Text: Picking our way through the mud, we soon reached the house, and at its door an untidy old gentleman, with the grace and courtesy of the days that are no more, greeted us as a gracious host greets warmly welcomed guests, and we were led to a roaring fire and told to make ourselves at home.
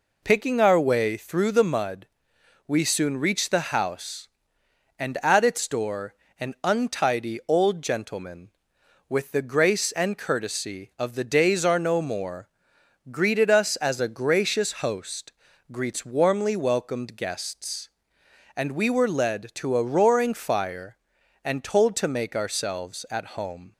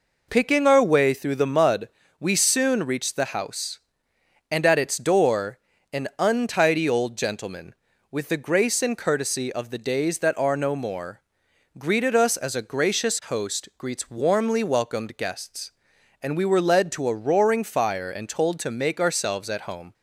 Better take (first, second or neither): second